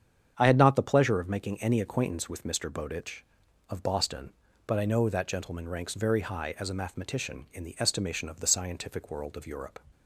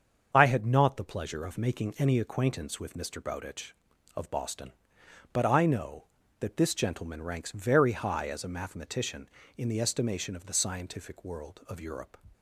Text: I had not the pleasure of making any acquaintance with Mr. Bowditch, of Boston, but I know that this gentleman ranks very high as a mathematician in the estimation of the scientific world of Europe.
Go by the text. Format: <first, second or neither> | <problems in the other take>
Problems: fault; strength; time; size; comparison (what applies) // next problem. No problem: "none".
second | starts louder than the rest; strong; until 1.3 s; 8 dB; also in the second // skips "this"; at 5.2 s